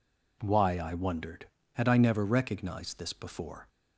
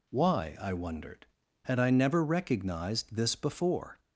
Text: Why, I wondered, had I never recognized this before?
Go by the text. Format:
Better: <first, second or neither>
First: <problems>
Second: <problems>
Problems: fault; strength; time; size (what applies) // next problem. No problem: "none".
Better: neither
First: none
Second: none